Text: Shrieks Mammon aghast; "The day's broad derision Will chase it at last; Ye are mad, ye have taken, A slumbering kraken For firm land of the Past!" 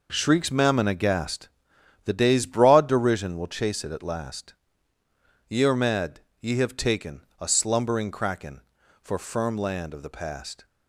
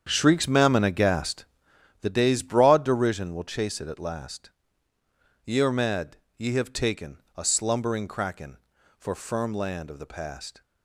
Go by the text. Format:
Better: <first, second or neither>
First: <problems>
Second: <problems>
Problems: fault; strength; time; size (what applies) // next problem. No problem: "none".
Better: first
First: none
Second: starts louder than the rest; strong; until 1.9 s; 8 dB